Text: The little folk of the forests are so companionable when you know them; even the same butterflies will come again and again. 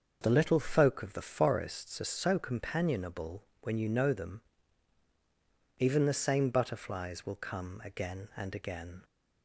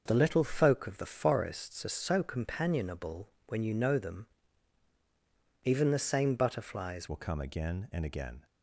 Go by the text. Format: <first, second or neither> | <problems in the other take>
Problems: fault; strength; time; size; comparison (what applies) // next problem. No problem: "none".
first | starts louder than the rest; noticeable; until 1.0 s; 6 dB; also in the first // pauses between "companionable" and "when"; slight; at 3.2 s; 0.18 s long; slight in the first // changes voice at "will"; from 7.0 s on; 1.4 s long